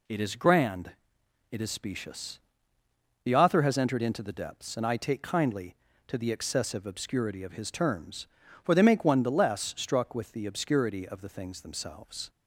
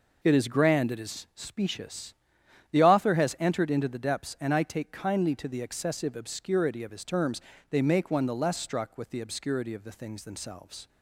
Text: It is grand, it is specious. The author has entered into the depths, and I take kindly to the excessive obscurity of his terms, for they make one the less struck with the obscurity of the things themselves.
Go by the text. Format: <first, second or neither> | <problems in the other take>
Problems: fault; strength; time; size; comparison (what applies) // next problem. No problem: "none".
first | skips "for"; at 7.5 s